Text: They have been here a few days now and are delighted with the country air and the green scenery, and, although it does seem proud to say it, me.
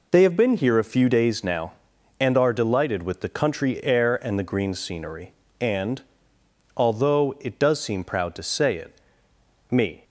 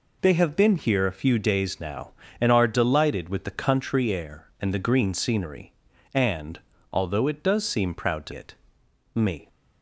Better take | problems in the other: first | skips "say"; at 8.3 s

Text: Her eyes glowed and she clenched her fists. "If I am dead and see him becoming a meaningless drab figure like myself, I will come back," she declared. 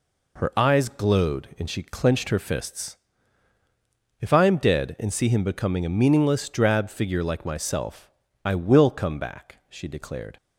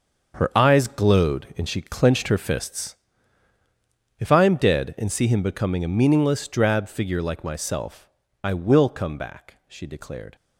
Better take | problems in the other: first | gets quieter; strong; throughout; 10.5 dB

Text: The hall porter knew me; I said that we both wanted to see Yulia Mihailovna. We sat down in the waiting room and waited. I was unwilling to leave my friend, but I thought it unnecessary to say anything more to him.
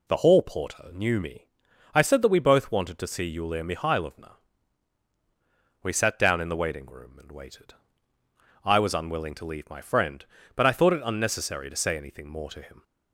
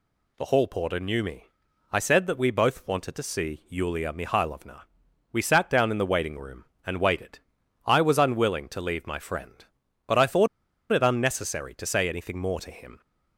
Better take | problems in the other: first | pauses between "thought" and "it"; at 10.4 s; 0.44 s long

